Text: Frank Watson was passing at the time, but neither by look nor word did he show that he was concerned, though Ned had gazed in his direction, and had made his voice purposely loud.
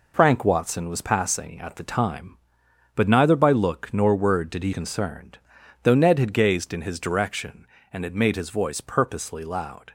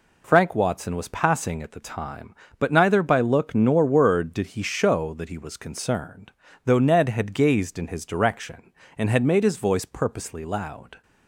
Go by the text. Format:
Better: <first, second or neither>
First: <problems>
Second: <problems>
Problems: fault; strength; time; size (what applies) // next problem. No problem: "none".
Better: second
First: skips "show that he was"; at 4.7 s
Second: none